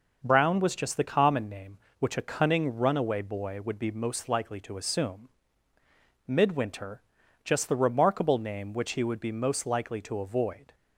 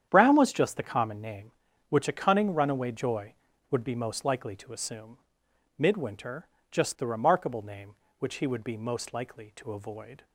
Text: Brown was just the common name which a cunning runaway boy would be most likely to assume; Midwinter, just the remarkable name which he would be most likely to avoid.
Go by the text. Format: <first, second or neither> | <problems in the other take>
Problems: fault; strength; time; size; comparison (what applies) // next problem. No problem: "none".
first | starts louder than the rest; strong; until 1.1 s; 9 dB // says "joy" for "boy"; at 2.9 s